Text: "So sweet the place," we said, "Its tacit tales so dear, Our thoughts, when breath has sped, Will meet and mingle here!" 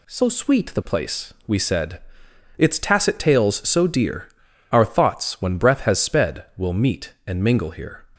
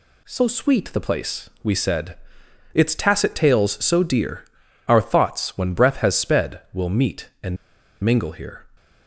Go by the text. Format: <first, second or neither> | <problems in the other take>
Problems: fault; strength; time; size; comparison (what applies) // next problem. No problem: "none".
first | pauses between "and" and "mingle"; noticeable; at 7.5 s; 0.47 s long